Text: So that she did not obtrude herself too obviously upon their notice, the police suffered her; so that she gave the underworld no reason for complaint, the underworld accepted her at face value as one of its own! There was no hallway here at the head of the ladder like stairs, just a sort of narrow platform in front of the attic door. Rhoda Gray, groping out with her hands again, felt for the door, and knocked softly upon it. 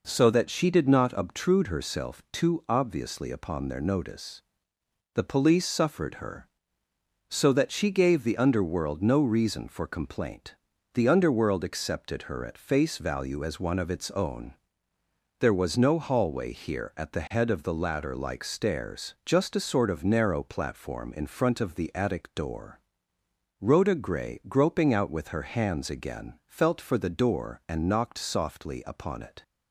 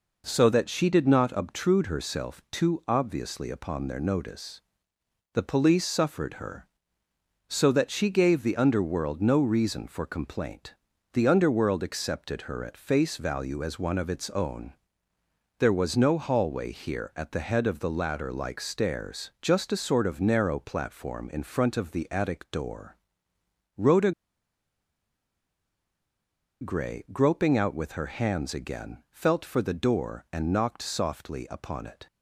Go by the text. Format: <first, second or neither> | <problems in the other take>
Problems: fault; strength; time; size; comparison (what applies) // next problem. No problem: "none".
first | pauses between "Rhoda" and "Gray"; strong; at 24.1 s; 2.5 s long